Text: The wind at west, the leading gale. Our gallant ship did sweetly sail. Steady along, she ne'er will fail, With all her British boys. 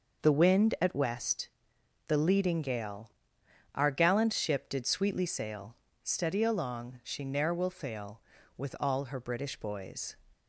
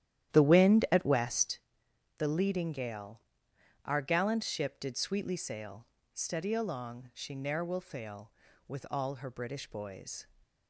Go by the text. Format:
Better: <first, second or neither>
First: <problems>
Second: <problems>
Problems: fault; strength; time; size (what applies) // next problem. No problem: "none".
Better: first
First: none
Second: starts louder than the rest; strong; until 1.7 s; 11.5 dB